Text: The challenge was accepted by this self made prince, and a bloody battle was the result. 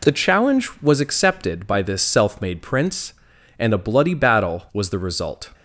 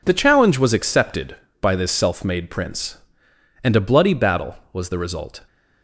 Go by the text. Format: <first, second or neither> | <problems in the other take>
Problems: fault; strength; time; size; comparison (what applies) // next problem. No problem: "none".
neither | none